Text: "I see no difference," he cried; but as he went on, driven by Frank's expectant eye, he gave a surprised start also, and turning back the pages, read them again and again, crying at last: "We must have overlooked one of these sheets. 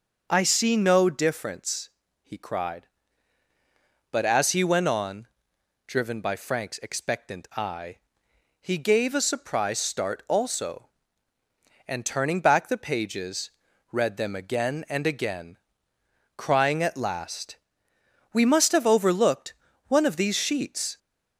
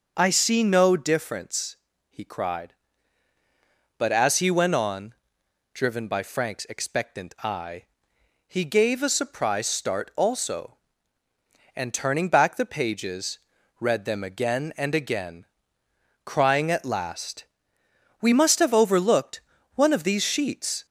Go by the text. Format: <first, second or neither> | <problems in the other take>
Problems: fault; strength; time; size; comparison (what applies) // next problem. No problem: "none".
neither | starts louder than the rest; the same in both // pauses between "overlooked" and "one"; slight; the same in both